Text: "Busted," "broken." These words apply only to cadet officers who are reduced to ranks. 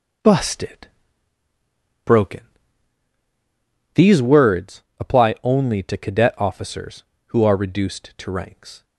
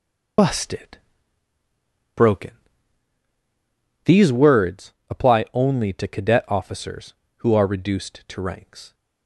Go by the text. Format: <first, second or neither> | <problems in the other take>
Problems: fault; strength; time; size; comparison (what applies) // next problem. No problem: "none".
first | loses the start of "Busted"; at 0.3 s; 60 ms // pauses between "words" and "apply"; slight; at 4.9 s; 0.16 s long; slight in the first